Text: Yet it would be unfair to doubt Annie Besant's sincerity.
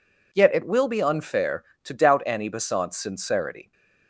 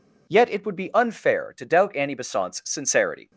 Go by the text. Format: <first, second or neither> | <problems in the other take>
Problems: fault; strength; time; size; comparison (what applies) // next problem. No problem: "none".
second | says "will" for "would"; at 0.6 s